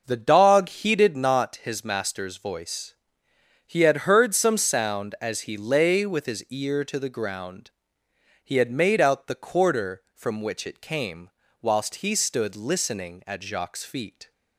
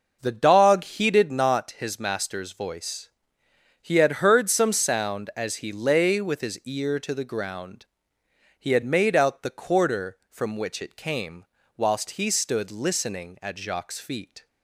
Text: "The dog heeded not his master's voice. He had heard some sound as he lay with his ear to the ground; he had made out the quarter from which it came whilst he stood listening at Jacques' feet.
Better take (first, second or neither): neither